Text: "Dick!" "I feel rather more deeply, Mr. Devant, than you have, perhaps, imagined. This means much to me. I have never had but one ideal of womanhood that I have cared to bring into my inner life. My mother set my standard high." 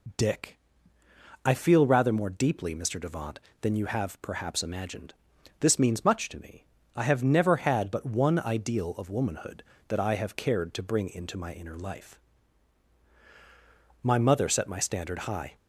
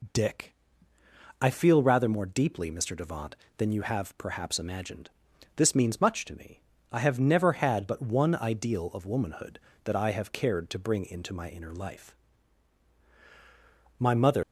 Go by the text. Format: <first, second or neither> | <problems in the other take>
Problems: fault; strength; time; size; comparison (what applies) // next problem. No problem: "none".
first | stops before "set my standard high"; at 14.4 s